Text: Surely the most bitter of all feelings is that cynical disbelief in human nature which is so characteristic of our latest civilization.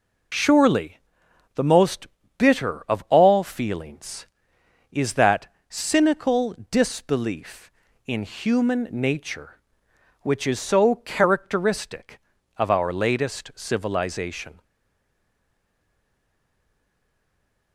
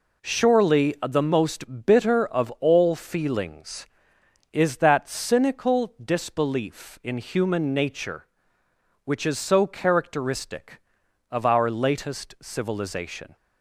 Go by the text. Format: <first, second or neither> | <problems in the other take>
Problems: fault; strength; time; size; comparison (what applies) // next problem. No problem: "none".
second | pauses between "Surely" and "the"; noticeable; at 0.9 s; 0.56 s long // pauses between "most" and "bitter"; slight; at 2.0 s; 0.32 s long // pauses between "that" and "cynical"; slight; at 5.4 s; 0.22 s long // pauses between "cynical" and "disbelief"; slight; at 6.5 s; 0.16 s long // stays silent after the last word; strong; from 14.6 s on; 3.1 s long